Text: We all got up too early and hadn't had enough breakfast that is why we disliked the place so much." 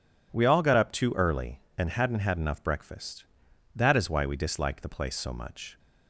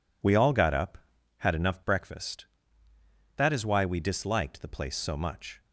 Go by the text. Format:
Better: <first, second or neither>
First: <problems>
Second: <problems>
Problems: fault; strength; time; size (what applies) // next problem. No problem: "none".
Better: first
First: none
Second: skips "too early and hadn't"; at 1.1 s